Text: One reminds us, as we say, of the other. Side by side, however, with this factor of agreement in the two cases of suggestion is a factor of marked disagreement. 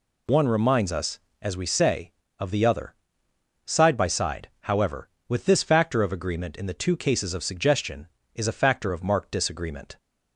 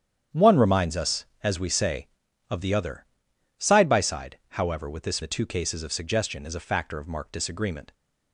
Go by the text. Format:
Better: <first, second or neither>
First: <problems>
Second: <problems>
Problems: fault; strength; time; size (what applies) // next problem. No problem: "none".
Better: first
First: none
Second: starts louder than the rest; strong; until 1.5 s; 9 dB // skips "factor of agreement in"; at 5.2 s